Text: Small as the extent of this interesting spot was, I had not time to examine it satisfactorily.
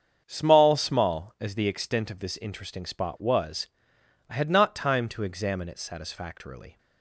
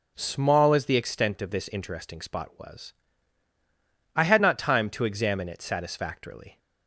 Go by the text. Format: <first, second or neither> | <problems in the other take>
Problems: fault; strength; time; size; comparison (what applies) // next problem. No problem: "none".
second | starts louder than the rest; strong; until 1.2 s; 7 dB; noticeable in the second // says "Small" twice; at 0.7 s